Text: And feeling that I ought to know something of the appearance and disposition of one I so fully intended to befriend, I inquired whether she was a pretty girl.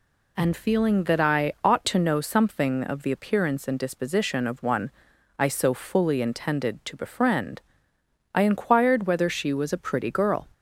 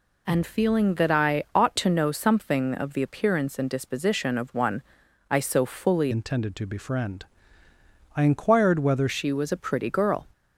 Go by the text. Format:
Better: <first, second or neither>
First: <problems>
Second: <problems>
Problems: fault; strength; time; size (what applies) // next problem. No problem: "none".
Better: first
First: pauses between "one" and "I"; noticeable; at 4.8 s; 0.48 s long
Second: pauses between "one" and "I"; noticeable; at 4.8 s; 0.48 s long // changes voice from "intended" to "whether"; from 6.1 to 9.0 s; 2.9 s long